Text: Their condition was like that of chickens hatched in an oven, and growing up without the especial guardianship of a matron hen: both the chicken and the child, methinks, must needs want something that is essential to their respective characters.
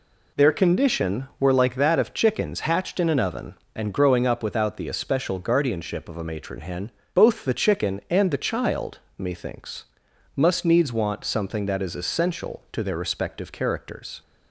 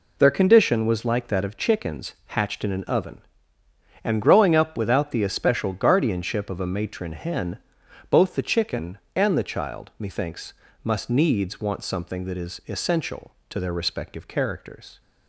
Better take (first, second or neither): second